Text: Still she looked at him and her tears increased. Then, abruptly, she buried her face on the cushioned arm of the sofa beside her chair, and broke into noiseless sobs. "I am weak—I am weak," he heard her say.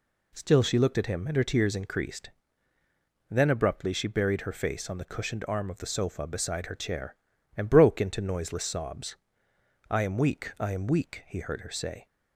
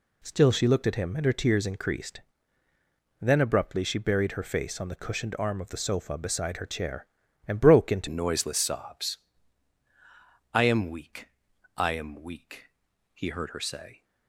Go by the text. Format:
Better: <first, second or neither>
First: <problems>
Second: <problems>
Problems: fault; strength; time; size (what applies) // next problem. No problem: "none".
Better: first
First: none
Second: changes voice at "noiseless"; from 8.0 s on; 6.0 s long